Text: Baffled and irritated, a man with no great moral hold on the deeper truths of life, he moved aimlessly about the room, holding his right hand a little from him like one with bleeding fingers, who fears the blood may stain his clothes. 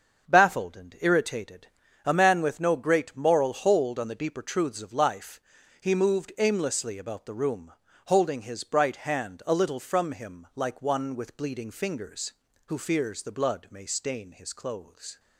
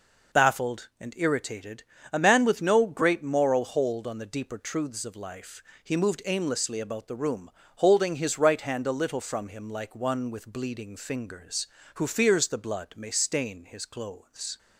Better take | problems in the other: second | starts louder than the rest; until 1.3 s; 6.5 dB // says "bright" for "right"; at 8.6 s

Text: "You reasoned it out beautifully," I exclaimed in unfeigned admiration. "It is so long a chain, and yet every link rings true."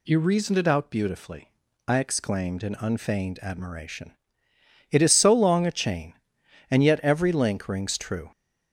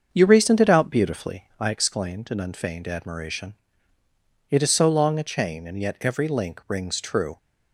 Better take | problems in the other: first | starts louder than the rest; until 1.7 s; 6.5 dB

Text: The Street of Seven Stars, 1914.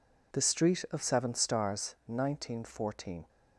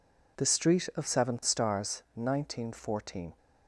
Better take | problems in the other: neither | none

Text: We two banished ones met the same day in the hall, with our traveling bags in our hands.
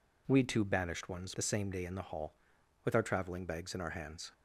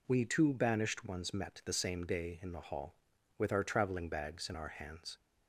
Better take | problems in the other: second | skips "met"; at 1.3 s

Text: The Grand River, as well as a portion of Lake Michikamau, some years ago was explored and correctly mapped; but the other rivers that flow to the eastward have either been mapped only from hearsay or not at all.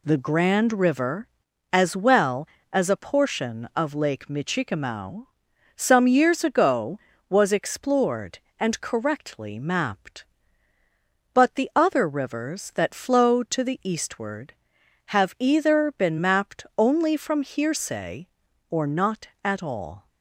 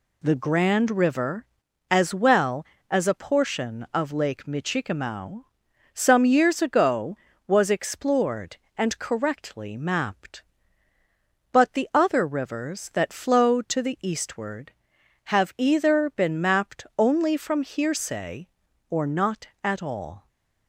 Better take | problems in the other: neither | none

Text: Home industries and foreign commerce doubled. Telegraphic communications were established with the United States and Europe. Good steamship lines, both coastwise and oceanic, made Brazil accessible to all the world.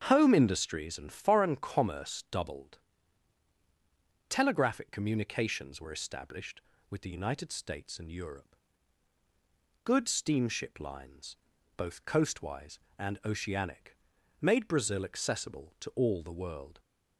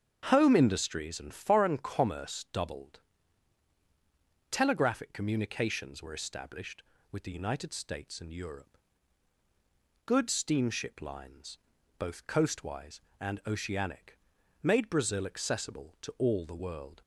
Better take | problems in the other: neither | starts louder than the rest; strong; the same in both

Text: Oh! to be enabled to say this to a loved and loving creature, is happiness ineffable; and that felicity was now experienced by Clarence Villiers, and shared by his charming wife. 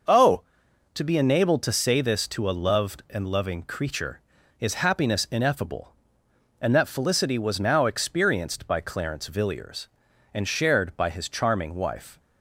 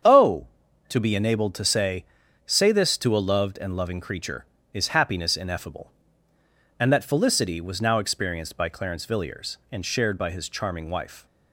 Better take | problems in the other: first | starts louder than the rest; strong; until 1.4 s; 7.5 dB // says "say" twice; at 2.4 s

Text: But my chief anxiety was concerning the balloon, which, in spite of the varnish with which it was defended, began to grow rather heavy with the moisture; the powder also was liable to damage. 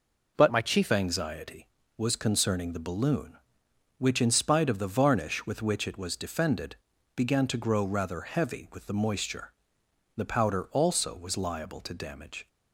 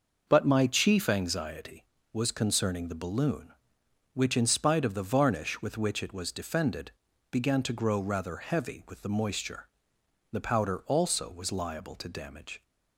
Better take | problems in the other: second | changes voice from "my" to "chief"; from 0.4 to 0.9 s; 0.5 s long

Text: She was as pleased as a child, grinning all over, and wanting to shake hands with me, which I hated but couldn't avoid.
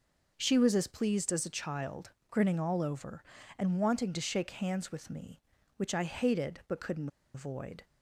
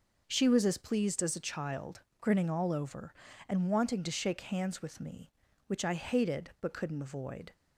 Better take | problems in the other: second | pauses between "couldn't" and "avoid"; slight; at 7.0 s; 0.26 s long

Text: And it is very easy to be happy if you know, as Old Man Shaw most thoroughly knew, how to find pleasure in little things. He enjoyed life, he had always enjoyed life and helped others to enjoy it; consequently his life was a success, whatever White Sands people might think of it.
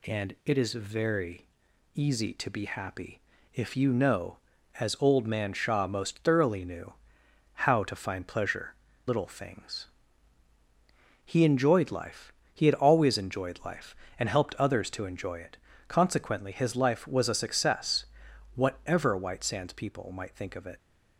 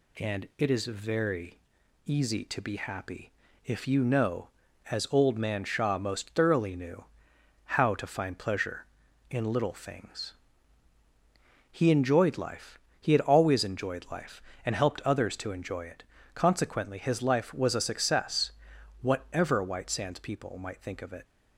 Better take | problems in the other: second | pauses between "very" and "easy"; noticeable; at 1.4 s; 0.50 s long; noticeable in the second // pauses between "happy" and "if"; slight; at 3.2 s; 0.32 s long; slight in the second // skips "in"; at 8.9 s

